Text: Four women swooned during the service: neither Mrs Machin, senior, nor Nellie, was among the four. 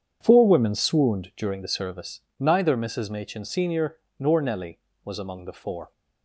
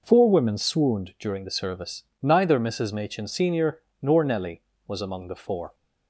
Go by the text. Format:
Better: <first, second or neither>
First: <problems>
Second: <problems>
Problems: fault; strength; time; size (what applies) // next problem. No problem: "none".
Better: second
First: starts louder than the rest; strong; until 1.9 s; 8 dB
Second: none